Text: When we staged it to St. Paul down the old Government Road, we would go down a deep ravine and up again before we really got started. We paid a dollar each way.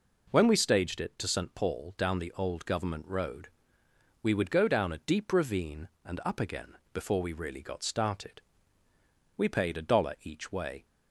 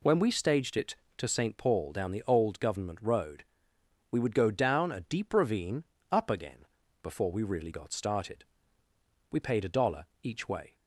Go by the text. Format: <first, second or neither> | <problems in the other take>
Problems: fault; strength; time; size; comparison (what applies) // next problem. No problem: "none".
first | skips "and"; at 5.9 s // pauses between "again" and "before"; at 6.6 s; 0.38 s long; slight in the first // pauses between "dollar" and "each"; slight; at 10.0 s; 0.16 s long